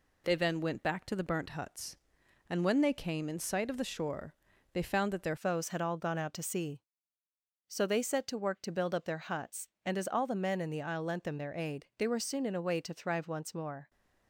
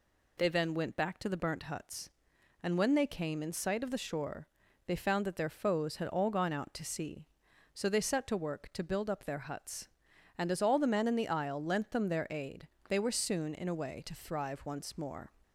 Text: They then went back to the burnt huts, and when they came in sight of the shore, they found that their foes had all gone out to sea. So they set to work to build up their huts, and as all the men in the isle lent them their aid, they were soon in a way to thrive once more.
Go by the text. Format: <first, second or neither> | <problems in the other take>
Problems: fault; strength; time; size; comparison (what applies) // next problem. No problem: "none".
second | changes voice at "foes"; from 5.3 s on; 8.5 s long